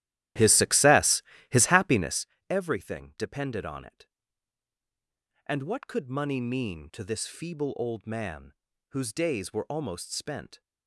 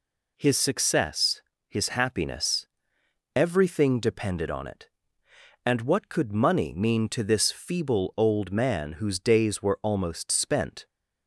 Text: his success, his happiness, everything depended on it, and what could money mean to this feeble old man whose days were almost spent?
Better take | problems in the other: second | starts louder than the rest; strong; until 2.3 s; 13.5 dB // pauses between "man" and "whose"; at 8.5 s; 0.38 s long

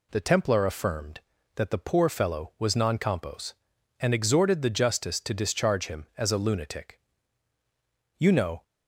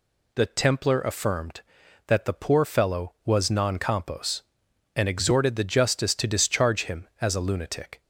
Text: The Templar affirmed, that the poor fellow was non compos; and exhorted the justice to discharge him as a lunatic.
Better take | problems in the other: second | goes on to say "You know"; slight; from 8.1 s on; 0.46 s long

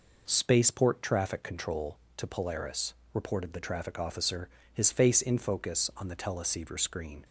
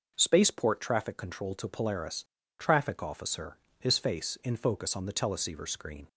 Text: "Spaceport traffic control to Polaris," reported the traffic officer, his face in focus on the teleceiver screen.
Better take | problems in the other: first | skips "reported the"; at 2.4 s

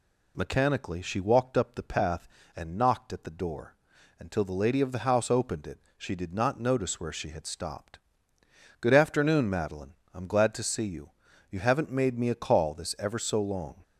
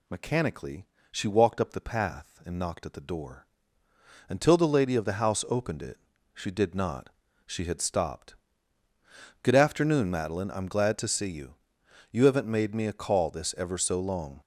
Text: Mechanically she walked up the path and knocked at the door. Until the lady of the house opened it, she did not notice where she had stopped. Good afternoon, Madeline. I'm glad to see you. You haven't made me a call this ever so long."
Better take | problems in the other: first | pauses between "Mechanically" and "she"; slight; at 0.8 s; 0.24 s long // skips "notice where"; at 7.2 s

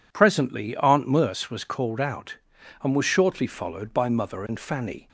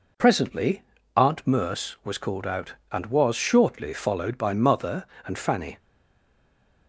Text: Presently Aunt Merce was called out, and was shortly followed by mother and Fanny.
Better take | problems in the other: first | pauses between "Presently" and "Aunt"; slight; at 0.8 s; 0.32 s long // stays silent after the last word; from 5.7 s on; 1.1 s long

